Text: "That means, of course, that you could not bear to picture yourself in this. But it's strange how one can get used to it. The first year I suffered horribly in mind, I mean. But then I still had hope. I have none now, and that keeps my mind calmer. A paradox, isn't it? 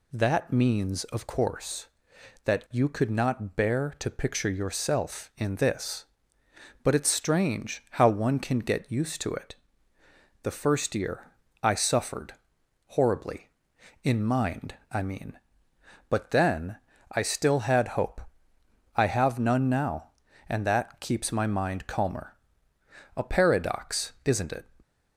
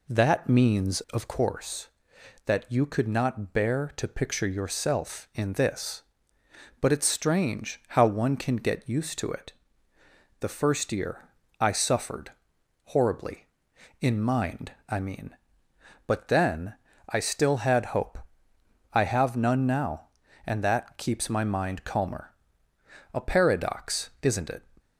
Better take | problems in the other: first | starts louder than the rest; slight; until 1.5 s; 3 dB // pauses between "year" and "I"; slight; at 11.2 s; 0.32 s long; slight in the first // pauses between "suffered" and "horribly"; noticeable; at 12.3 s; 0.54 s long; noticeable in the first // pauses between "then" and "I"; slight; at 16.7 s; 0.36 s long; slight in the first

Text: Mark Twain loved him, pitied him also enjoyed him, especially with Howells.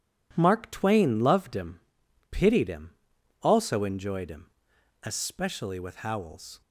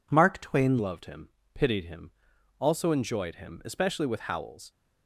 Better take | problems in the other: first | changes voice at "loved"; from 0.7 s on; 4.0 s long // pauses between "him" and "also"; noticeable; at 2.1 s; 0.48 s long; noticeable in the first

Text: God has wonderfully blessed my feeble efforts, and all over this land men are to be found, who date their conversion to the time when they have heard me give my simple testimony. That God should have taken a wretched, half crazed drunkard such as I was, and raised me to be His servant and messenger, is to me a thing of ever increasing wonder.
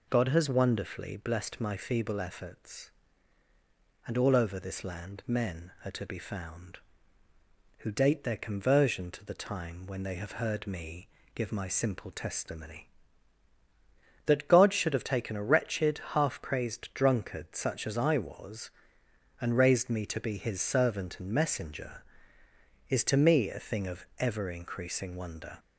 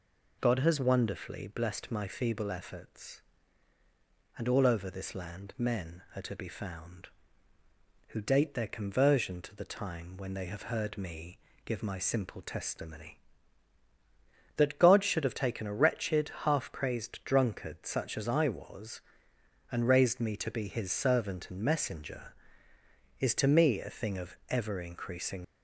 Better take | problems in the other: first | pauses between "me" and "give"; slight; at 11.3 s; 0.26 s long; slight in the first // stops before "wonder"; at 25.4 s

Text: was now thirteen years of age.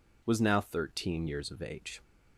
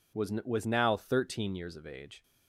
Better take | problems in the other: first | says "was" twice; at 0.4 s

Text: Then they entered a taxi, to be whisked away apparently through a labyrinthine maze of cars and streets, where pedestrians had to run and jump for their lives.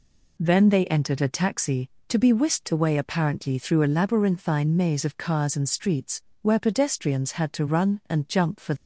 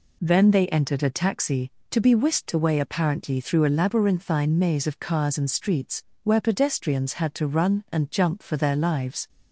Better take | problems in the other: second | stops before "their lives"; at 8.7 s

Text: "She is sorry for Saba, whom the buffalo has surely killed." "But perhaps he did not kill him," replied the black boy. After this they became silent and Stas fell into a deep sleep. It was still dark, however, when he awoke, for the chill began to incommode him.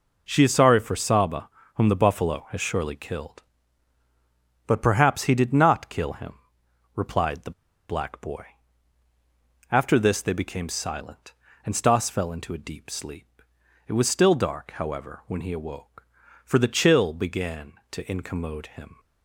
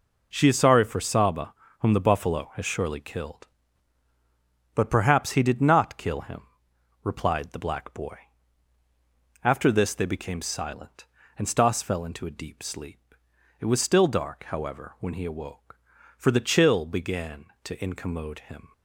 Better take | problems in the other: second | pauses between "the" and "black"; at 7.5 s; 0.39 s long

